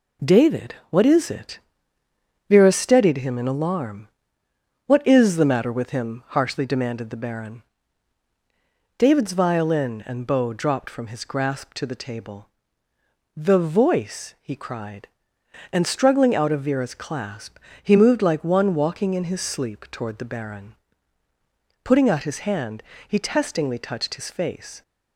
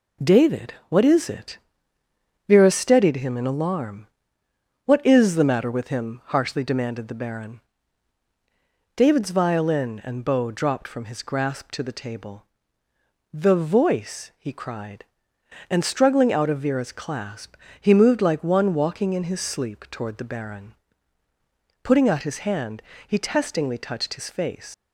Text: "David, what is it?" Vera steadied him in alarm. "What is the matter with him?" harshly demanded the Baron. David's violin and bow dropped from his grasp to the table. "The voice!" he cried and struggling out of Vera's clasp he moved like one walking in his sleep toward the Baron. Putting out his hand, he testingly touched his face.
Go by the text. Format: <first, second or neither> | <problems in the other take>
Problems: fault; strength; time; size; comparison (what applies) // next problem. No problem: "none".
first | pauses between "clasp" and "he"; slight; at 17.5 s; 0.26 s long; slight in the first // leaves "face" unfinished; at 24.7 s; 70 ms